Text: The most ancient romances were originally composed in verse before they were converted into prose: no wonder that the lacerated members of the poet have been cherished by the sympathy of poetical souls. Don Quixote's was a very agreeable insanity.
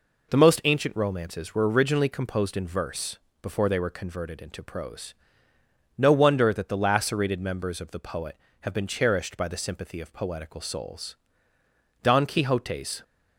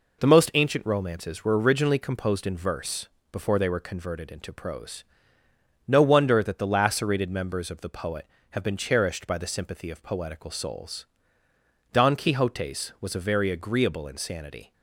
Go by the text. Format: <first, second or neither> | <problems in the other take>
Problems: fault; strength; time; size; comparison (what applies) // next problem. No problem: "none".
second | pauses between "verse" and "before"; slight; at 3.1 s; 0.24 s long; slight in the second // stops before "was a very agreeable insanity"; at 13.0 s